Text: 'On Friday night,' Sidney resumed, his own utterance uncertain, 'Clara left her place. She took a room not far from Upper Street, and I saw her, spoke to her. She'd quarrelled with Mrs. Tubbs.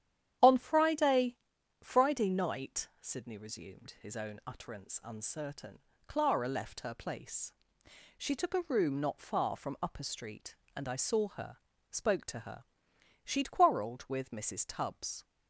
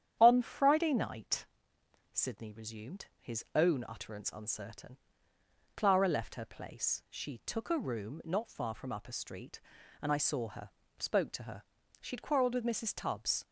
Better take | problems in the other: second | starts louder than the rest; strong; until 1.8 s; 10.5 dB; strong in the second // says "Friday" twice; at 1.8 s

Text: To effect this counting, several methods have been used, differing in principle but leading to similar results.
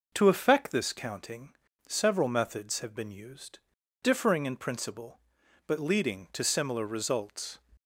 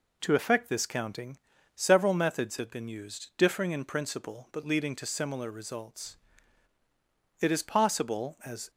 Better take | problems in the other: first | goes on to say "It is possible as"; noticeable; from 7.4 s on; 1.2 s long

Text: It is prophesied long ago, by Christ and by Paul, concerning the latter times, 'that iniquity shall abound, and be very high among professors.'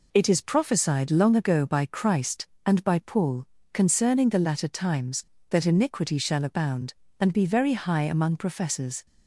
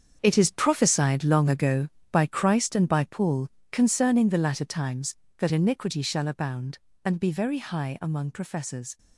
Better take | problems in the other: first | gets quieter; strong; throughout; 12 dB

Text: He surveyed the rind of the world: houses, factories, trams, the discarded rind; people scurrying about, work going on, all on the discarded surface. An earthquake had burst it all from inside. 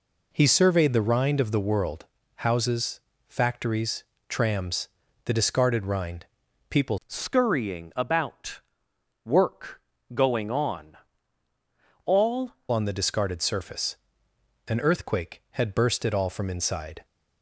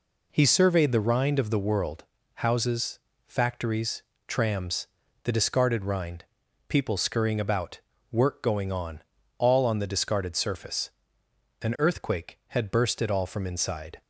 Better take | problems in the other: second | changes voice from "scurrying" to "all"; from 7.0 to 12.5 s; 5.5 s long // pauses between "work" and "going"; slight; at 9.8 s; 0.34 s long

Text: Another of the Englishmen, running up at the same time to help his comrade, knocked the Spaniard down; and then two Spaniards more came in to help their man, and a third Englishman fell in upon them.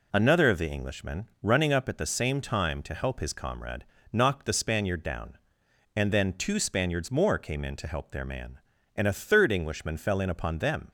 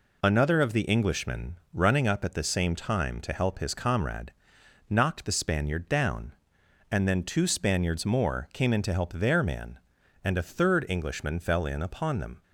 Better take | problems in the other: neither | none

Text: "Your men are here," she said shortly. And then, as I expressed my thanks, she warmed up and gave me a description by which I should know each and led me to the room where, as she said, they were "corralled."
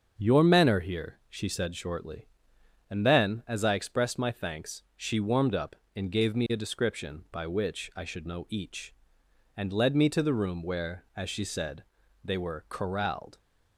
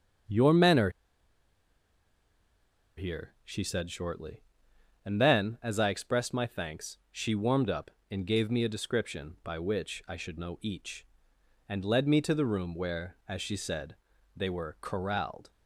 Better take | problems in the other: first | starts louder than the rest; until 3.4 s; 6.5 dB; also in the first // pauses between "are" and "here"; strong; at 0.8 s; 2.0 s long

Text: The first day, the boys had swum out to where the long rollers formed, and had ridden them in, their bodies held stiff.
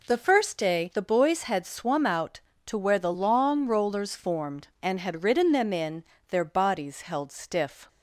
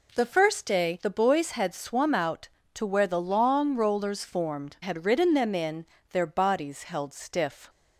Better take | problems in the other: first | skips "and"; at 4.7 s

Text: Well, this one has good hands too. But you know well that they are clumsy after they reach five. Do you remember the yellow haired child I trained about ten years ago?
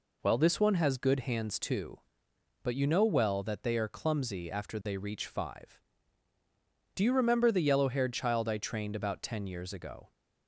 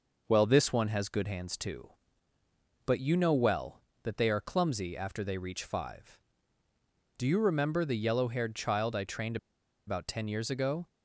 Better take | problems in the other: first | pauses between "trained" and "about"; noticeable; at 9.3 s; 0.50 s long

